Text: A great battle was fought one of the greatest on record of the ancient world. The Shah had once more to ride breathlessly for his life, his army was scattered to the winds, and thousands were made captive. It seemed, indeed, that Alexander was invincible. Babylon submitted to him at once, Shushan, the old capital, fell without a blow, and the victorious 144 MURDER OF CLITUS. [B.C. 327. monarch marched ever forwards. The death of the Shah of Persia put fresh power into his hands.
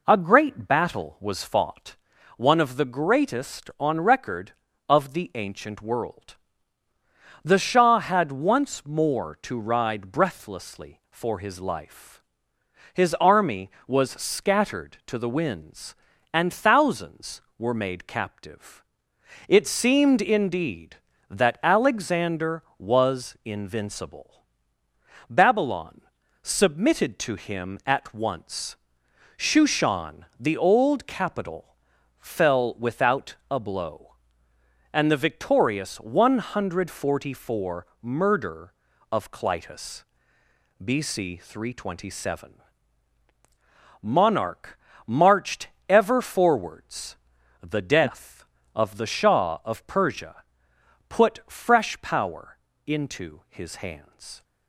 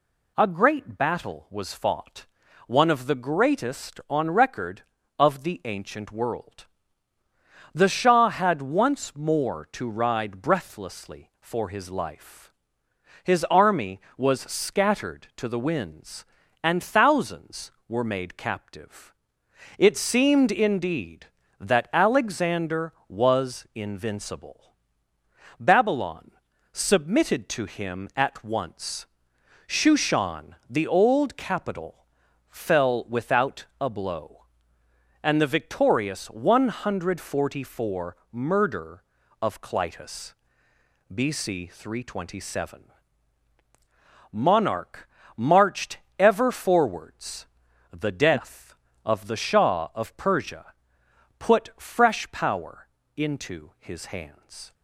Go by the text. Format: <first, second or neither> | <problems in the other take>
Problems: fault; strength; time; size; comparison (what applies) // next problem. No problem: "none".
second | starts louder than the rest; noticeable; until 1.8 s; 4 dB // pauses between "fought" and "one"; at 1.9 s; 0.40 s long; also in the second // pauses between "Babylon" and "submitted"; at 26.0 s; 0.40 s long; also in the second // pauses between "monarch" and "marched"; slight; at 44.7 s; 0.30 s long; slight in the second // pauses between "marched" and "ever"; slight; at 45.6 s; 0.22 s long; slight in the second // pauses between "Persia" and "put"; noticeable; at 50.4 s; 0.66 s long; noticeable in the second // pauses between "power" and "into"; slight; at 52.5 s; 0.28 s long; slight in the second